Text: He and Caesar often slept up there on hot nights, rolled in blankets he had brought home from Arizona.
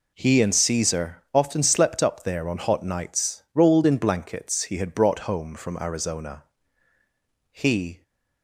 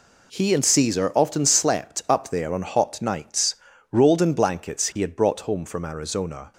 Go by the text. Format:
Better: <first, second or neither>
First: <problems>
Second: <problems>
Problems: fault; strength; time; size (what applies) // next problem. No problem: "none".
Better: second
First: goes on to say "He"; from 7.5 s on; 0.52 s long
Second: none